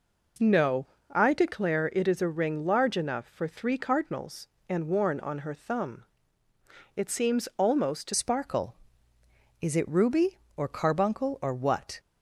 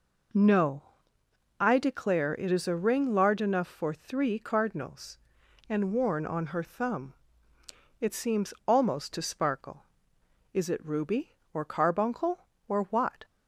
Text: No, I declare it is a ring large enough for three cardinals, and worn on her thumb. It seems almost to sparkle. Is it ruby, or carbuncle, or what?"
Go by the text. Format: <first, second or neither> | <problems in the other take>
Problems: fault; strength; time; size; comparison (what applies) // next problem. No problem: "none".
second | changes voice at "sparkle"; from 8.1 s on; 3.8 s long